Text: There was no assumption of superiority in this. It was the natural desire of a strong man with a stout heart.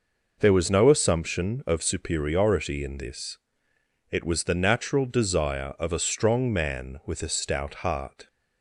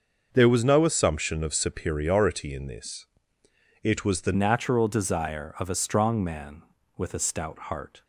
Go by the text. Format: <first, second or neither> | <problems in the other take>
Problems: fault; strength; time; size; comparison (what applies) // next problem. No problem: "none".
first | starts louder than the rest; noticeable; until 1.3 s; 6 dB // changes voice at "natural"; from 4.3 s on; 3.7 s long